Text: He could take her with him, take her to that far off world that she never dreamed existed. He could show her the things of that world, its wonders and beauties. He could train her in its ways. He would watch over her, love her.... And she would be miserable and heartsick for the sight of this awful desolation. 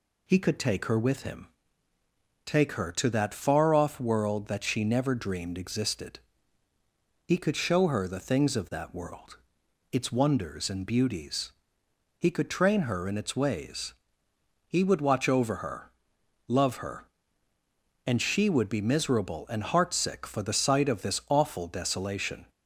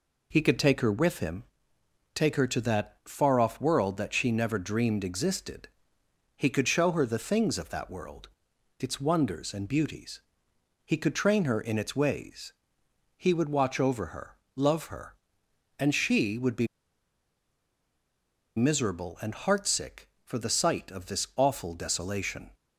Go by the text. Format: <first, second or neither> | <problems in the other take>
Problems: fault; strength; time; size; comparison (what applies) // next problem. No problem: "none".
first | pauses between "be" and "miserable"; strong; at 16.6 s; 1.8 s long